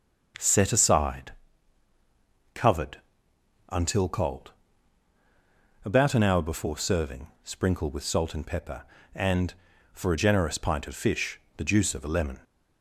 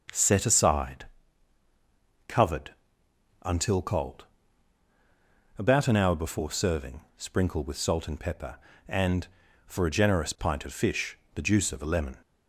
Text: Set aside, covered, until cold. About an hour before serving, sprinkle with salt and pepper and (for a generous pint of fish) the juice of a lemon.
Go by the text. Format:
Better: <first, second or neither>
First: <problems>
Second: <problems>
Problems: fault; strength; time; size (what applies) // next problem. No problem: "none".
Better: neither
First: none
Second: none